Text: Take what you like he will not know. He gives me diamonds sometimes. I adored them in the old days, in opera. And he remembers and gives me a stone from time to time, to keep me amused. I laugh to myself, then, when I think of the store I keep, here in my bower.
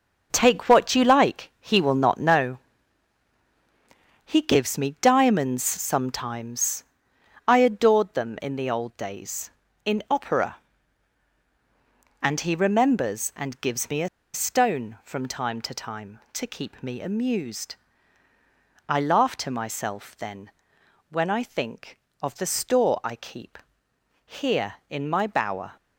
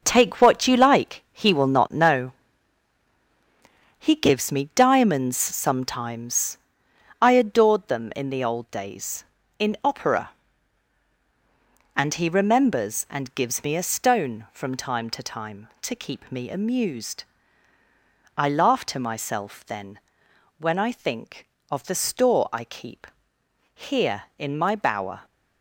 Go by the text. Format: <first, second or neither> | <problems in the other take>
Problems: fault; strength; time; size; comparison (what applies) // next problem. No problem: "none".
second | starts louder than the rest; until 1.3 s; 6 dB; also in the second // pauses between "a" and "stone"; slight; at 14.0 s; 0.25 s long